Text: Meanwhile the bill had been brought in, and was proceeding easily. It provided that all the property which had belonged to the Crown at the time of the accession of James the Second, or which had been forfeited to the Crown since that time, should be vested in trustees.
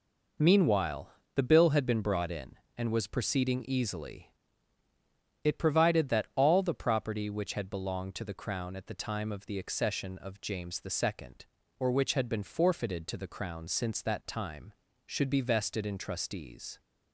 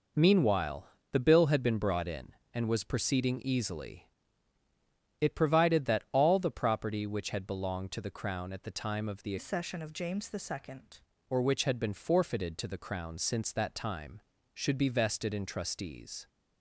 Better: first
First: pauses between "Meanwhile" and "the"; slight; at 1.0 s; 0.24 s long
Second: pauses between "Meanwhile" and "the"; slight; at 0.8 s; 0.24 s long // changes voice from "accession" to "Second"; from 9.3 to 11.0 s; 1.7 s long

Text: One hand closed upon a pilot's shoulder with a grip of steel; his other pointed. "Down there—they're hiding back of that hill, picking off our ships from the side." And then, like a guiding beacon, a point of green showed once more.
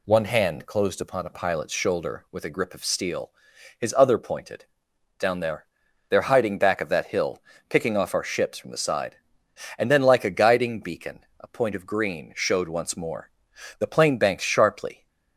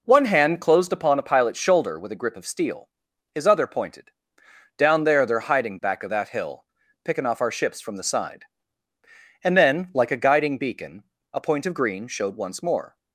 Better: second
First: goes on to say "The plane banked sharply"; noticeable; from 13.7 s on; 1.2 s long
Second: none

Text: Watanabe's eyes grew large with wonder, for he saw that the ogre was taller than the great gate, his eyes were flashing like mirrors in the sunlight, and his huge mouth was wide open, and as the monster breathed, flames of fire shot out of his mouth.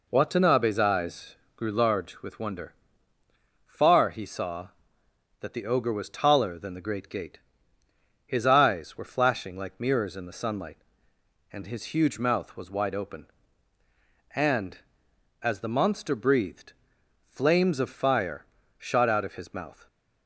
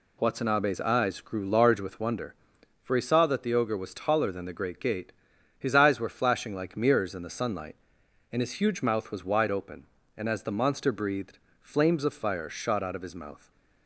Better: second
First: pauses between "eyes" and "grew"; slight; at 1.3 s; 0.22 s long // says "far" for "for"; at 3.6 s // pauses between "fire" and "shot"; slight; at 18.4 s; 0.34 s long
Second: none

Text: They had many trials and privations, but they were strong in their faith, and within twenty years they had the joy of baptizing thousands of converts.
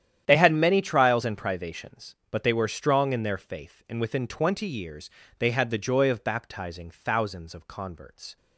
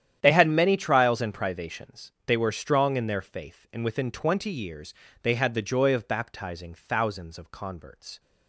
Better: first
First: starts louder than the rest; strong; until 1.2 s; 10 dB // pauses between "years" and "they"; slight; at 5.0 s; 0.30 s long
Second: starts louder than the rest; strong; until 1.2 s; 10 dB // skips "but"; at 2.2 s // pauses between "years" and "they"; slight; at 4.9 s; 0.30 s long

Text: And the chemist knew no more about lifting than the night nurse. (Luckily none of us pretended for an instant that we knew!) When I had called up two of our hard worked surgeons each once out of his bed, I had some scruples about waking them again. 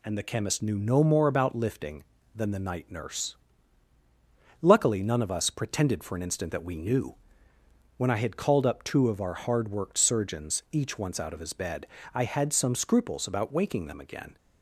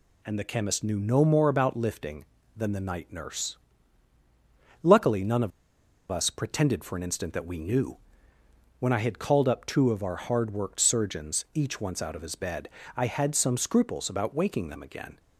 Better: first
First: none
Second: pauses between "of" and "us"; noticeable; at 5.5 s; 0.60 s long

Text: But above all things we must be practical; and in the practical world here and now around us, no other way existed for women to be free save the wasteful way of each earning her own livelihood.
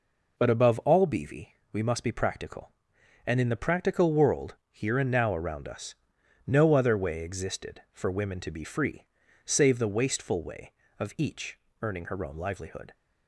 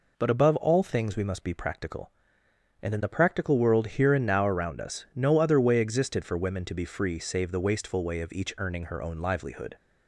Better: second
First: says "beavy" for "things"; at 1.0 s // pauses between "world" and "here"; slight; at 4.5 s; 0.16 s long // pauses between "free" and "save"; at 9.0 s; 0.40 s long // pauses between "each" and "earning"; slight; at 11.5 s; 0.24 s long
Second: none

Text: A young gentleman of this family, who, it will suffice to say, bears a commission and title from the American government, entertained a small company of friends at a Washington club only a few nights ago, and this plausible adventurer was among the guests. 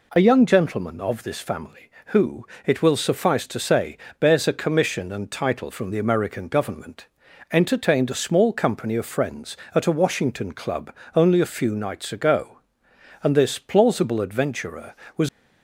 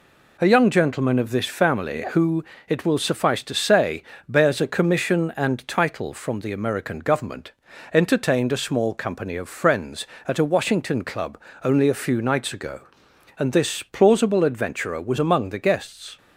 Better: second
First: pauses between "club" and "only"; slight; at 10.9 s; 0.22 s long // stops before "among the guests"; at 15.2 s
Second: pauses between "club" and "only"; slight; at 11.3 s; 0.24 s long

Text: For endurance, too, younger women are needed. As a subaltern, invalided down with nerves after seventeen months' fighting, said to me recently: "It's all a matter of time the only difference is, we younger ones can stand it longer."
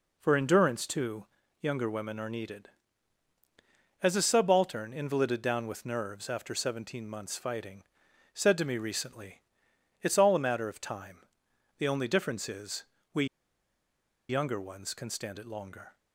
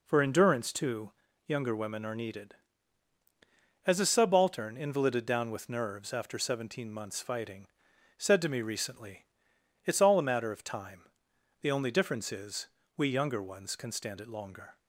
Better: second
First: pauses between "time" and "the"; noticeable; at 11.2 s; 0.54 s long // pauses between "we" and "younger"; at 13.2 s; 1.0 s long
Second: pauses between "time" and "the"; noticeable; at 11.0 s; 0.54 s long

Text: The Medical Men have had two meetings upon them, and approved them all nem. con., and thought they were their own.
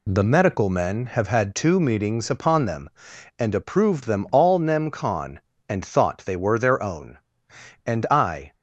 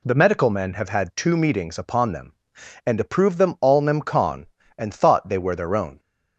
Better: second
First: goes on to say "And I"; noticeable; from 7.8 s on; 0.68 s long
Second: none

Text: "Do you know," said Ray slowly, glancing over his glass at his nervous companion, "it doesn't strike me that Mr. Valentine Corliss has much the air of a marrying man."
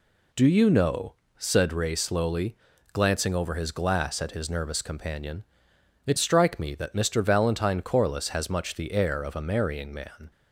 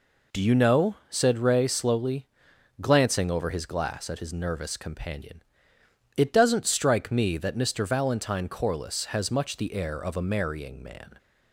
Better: second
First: skips "doesn't"; at 6.1 s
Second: none

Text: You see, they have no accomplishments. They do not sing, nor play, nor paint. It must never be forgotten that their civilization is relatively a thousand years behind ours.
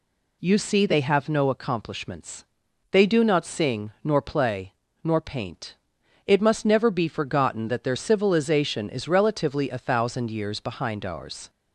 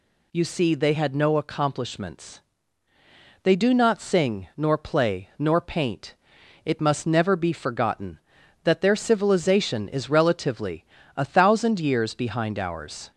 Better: first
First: none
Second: says "had" for "have"; at 0.9 s // pauses between "relatively" and "a"; slight; at 10.8 s; 0.32 s long

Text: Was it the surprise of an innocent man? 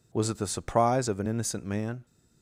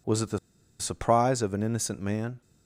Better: first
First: none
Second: pauses between "the" and "surprise"; at 0.3 s; 0.42 s long

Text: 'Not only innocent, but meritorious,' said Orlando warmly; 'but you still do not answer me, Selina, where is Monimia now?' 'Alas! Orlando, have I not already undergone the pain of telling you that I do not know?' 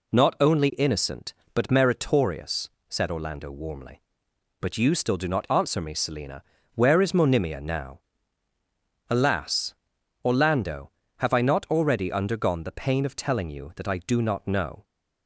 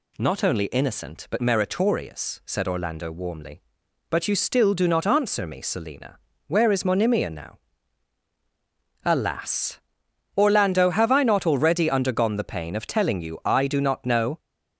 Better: first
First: none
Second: skips "that"; at 13.4 s

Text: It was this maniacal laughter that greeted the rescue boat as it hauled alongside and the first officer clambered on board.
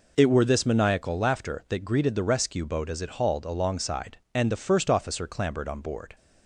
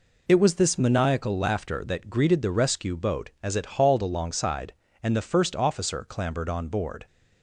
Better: second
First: says "were" for "was"; at 0.2 s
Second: none

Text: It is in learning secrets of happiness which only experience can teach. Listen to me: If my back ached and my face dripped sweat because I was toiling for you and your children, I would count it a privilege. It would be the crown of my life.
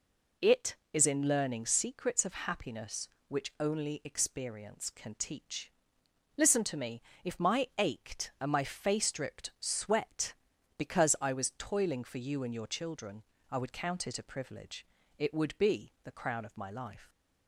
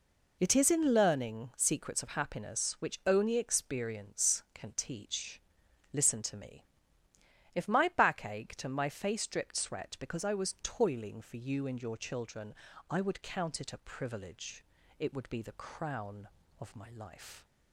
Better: second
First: skips "back"; at 7.7 s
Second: none

